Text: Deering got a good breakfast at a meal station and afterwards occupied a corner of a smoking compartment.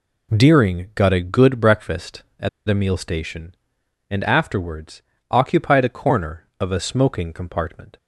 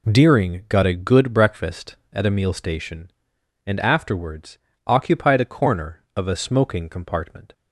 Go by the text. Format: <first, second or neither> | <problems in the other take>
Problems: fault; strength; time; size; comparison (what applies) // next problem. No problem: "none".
second | pauses between "at" and "a"; slight; at 2.4 s; 0.19 s long // pauses between "afterwards" and "occupied"; slight; at 5.0 s; 0.28 s long; slight in the second